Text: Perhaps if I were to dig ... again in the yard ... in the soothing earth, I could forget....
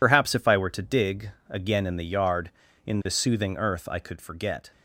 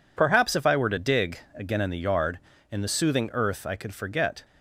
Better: second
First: loses the start of "Perhaps"; at 0.0 s; 60 ms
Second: none

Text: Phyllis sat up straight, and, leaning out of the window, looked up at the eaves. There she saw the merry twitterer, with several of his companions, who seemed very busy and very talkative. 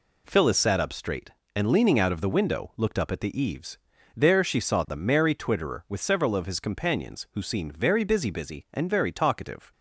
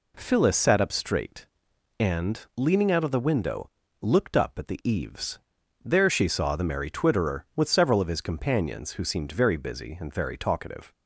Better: second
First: says "busy" twice; at 8.2 s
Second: none

